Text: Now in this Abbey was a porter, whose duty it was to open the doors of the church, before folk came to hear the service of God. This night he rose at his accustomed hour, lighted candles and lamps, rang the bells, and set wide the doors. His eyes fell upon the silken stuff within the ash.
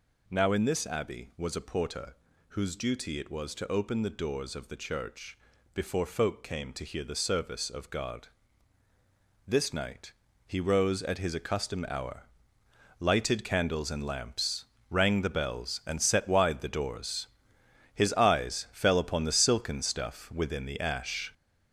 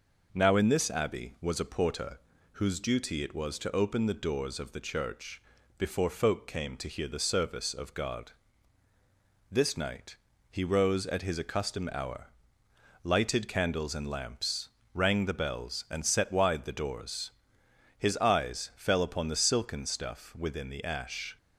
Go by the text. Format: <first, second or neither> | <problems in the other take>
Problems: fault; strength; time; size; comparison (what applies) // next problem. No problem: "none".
second | gets louder; noticeable; throughout; 6 dB // pauses between "night" and "he"; slight; at 10.1 s; 0.34 s long; slight in the second